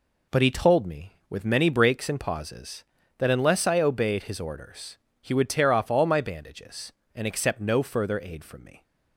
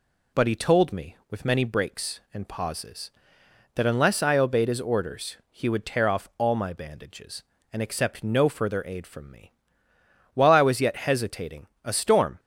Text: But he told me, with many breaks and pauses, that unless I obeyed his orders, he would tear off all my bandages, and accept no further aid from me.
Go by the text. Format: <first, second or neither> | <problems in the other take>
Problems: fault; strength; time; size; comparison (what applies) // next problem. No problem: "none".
first | goes on to say "While I was yet hesitating a storm"; strong; from 10.3 s on; 2.0 s long